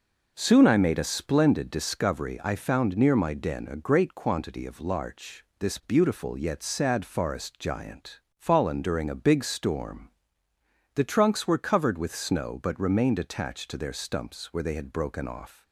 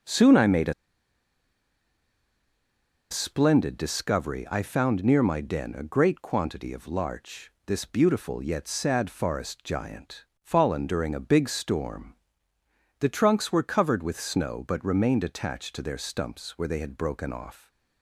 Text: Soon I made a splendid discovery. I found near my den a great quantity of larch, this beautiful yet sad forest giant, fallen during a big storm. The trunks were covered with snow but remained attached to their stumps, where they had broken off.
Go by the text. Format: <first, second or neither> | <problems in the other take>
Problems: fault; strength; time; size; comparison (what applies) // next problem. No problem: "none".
first | pauses between "a" and "splendid"; strong; at 0.7 s; 2.3 s long